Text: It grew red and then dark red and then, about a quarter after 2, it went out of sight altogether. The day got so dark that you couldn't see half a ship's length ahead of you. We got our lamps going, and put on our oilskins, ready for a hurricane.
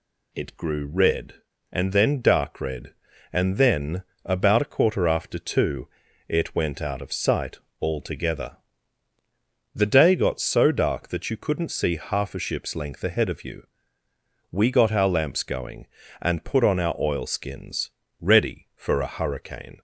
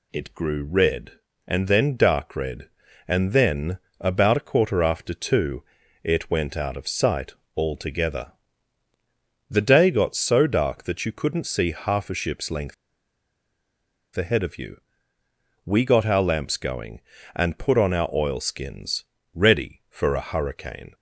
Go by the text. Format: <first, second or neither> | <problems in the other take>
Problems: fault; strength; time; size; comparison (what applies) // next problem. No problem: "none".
first | pauses between "sight" and "altogether"; slight; at 7.3 s; 0.24 s long; slight in the first // pauses between "length" and "ahead"; strong; at 12.7 s; 1.4 s long